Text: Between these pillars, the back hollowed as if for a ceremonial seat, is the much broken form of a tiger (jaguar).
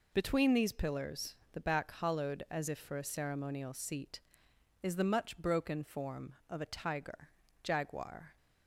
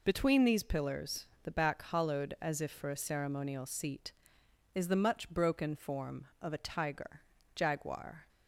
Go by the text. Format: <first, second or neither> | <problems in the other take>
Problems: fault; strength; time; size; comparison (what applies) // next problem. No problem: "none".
neither | none